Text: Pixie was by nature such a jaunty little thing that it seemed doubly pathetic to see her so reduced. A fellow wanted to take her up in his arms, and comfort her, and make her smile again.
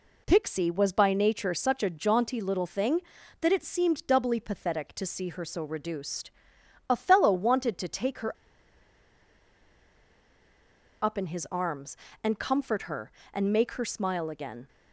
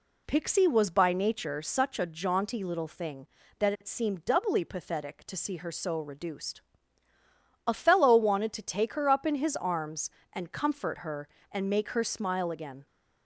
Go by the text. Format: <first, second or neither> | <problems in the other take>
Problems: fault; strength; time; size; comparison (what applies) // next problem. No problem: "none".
second | pauses between "her" and "up"; strong; at 8.3 s; 2.6 s long